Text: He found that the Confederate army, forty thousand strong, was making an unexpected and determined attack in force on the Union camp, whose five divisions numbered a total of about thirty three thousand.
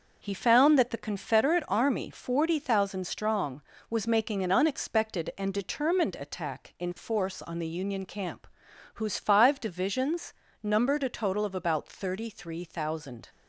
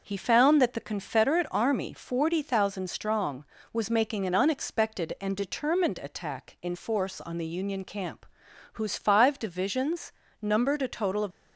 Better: first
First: starts louder than the rest; until 1.2 s; 6.5 dB // pauses between "divisions" and "numbered"; slight; at 10.3 s; 0.30 s long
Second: starts louder than the rest; until 1.0 s; 6 dB // pauses between "divisions" and "numbered"; slight; at 10.1 s; 0.30 s long // stops before "about thirty three thousand"; at 11.3 s

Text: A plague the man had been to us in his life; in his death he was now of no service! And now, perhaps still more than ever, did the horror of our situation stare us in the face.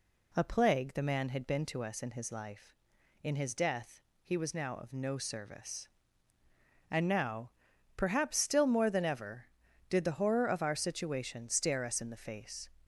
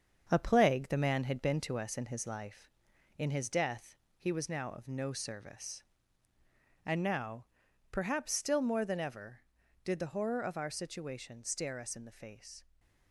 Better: first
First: pauses between "death" and "he"; slight; at 4.0 s; 0.22 s long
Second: gets quieter; noticeable; throughout; 5 dB // pauses between "death" and "he"; slight; at 3.9 s; 0.22 s long

